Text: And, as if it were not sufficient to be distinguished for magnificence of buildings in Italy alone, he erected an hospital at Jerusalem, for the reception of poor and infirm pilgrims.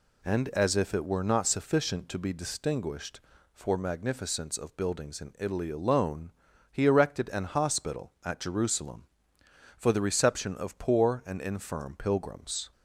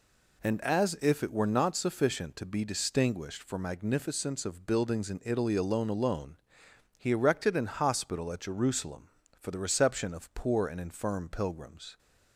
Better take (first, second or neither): first